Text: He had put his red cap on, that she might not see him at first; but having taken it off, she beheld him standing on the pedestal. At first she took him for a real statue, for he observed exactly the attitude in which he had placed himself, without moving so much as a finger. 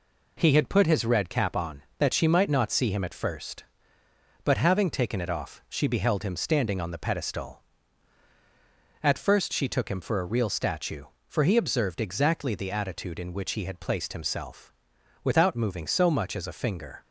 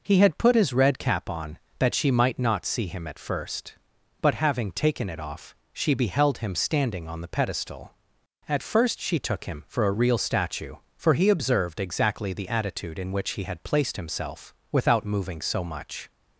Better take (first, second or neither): first